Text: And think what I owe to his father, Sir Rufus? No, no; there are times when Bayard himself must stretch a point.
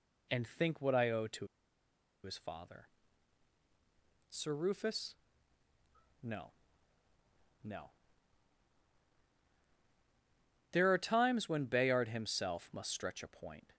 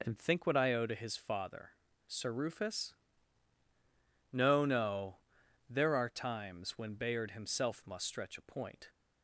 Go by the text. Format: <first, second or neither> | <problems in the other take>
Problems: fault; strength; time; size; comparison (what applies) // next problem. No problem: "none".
second | pauses between "to" and "his"; noticeable; at 1.4 s; 0.76 s long